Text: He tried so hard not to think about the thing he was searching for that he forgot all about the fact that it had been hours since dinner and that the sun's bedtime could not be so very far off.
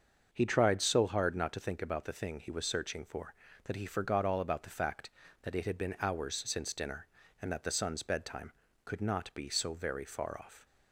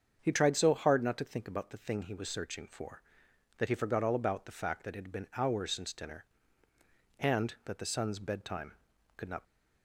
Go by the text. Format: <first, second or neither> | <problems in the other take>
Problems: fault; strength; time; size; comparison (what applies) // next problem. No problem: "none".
first | starts louder than the rest; strong; until 1.2 s; 7 dB; also in the first // stops before "be so very far off"; at 9.4 s